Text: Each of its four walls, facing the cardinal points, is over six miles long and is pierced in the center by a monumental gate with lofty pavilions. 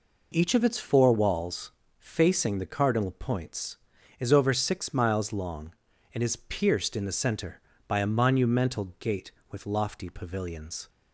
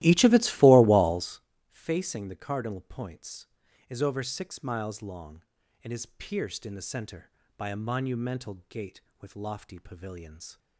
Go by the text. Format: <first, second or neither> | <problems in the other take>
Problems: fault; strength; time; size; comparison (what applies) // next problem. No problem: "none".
first | starts louder than the rest; strong; until 1.4 s; 16 dB